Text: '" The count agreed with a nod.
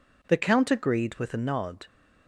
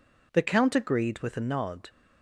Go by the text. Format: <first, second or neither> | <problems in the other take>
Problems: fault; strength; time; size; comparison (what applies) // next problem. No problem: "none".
neither | none